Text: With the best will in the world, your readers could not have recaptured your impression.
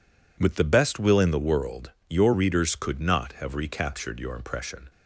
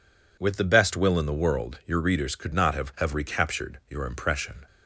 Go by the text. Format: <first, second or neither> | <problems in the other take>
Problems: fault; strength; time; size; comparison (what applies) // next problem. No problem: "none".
first | says "have" twice; at 2.9 s